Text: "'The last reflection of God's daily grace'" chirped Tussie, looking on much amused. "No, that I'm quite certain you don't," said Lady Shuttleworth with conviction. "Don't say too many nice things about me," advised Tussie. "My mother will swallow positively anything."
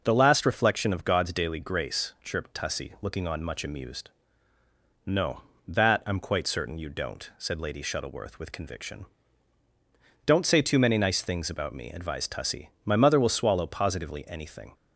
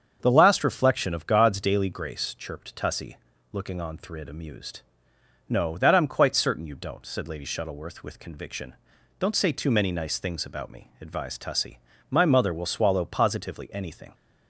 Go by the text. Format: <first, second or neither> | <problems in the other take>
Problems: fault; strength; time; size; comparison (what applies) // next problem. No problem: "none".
first | starts louder than the rest; strong; until 1.2 s; 7.5 dB // says "thrid" for "much"; at 3.9 s